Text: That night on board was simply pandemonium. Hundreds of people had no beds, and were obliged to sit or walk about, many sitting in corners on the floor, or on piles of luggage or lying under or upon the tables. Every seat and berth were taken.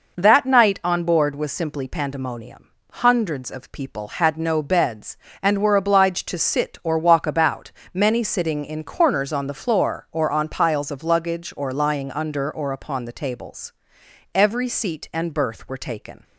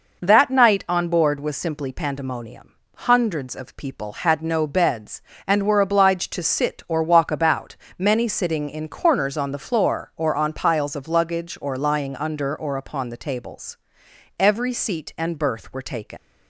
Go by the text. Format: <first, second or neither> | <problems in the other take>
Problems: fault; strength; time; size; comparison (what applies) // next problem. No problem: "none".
first | leaves "taken" unfinished; at 16.1 s; 105 ms